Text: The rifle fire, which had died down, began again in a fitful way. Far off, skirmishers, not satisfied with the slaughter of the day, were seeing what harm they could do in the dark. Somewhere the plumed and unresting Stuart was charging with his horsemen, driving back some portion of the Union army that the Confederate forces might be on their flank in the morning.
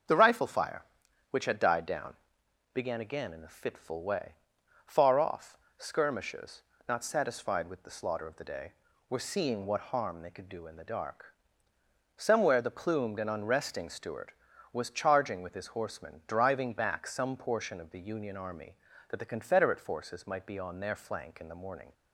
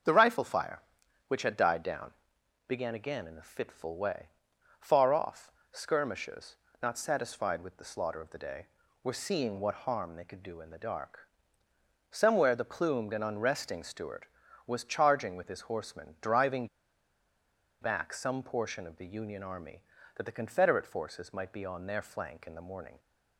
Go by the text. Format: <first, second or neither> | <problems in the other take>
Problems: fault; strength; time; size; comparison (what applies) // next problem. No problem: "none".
first | starts louder than the rest; until 1.5 s; 6.5 dB; also in the first // pauses between "driving" and "back"; at 16.6 s; 1.1 s long